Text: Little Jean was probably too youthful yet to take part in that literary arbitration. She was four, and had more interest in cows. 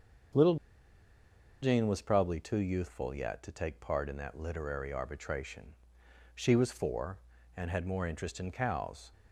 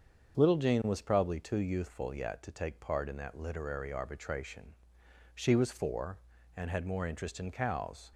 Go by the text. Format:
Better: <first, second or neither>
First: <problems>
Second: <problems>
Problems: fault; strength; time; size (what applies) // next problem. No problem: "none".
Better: second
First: starts louder than the rest; until 2.4 s; 7 dB // pauses between "Little" and "Jean"; at 0.5 s; 1.0 s long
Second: starts louder than the rest; until 1.4 s; 7 dB